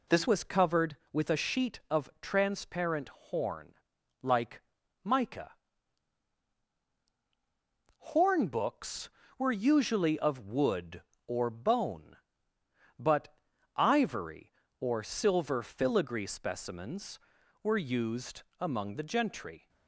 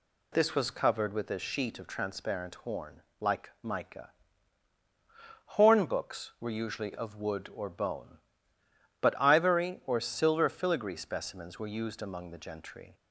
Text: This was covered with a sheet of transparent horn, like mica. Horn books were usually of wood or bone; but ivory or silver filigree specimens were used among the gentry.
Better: second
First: changes voice at "was"; from 0.2 s on; 19.4 s long // pauses between "like" and "mica"; at 4.6 s; 0.42 s long // pauses between "but" and "ivory"; at 13.3 s; 0.38 s long // pauses between "used" and "among"; slight; at 18.4 s; 0.18 s long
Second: none

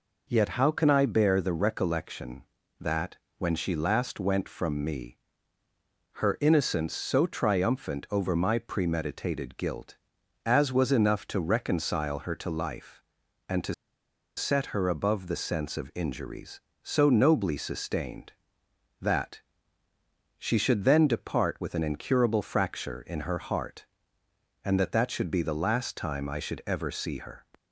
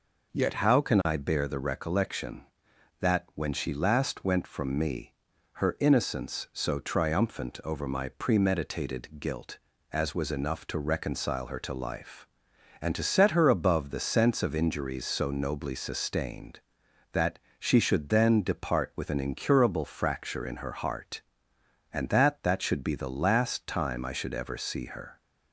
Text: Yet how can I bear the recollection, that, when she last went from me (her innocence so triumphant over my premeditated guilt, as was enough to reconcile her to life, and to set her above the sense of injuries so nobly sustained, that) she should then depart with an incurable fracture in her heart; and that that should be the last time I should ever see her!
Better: second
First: pauses between "to" and "set"; noticeable; at 13.7 s; 0.64 s long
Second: none

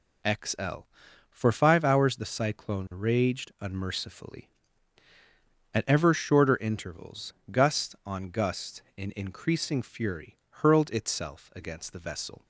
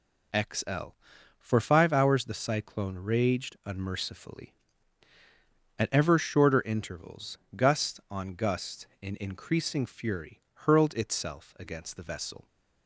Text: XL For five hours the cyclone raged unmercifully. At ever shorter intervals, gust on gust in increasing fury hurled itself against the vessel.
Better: neither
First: none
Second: none

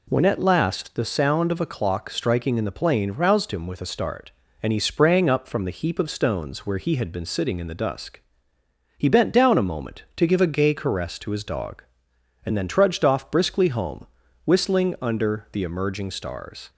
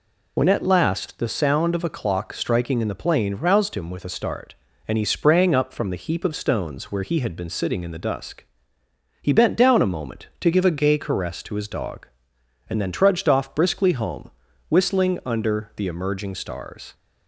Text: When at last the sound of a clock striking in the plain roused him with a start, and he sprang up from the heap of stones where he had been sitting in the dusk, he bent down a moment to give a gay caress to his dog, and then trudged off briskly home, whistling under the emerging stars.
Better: first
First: none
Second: loses the start of "When"; at 0.3 s; 60 ms

